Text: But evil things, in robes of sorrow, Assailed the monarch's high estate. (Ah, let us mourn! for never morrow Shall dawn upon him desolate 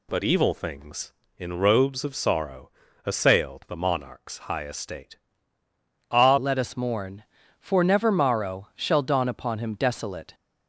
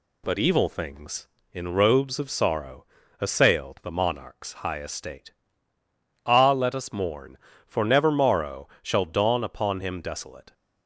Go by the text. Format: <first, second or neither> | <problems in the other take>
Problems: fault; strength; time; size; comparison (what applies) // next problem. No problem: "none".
second | changes voice at "let"; from 6.3 s on; 4.0 s long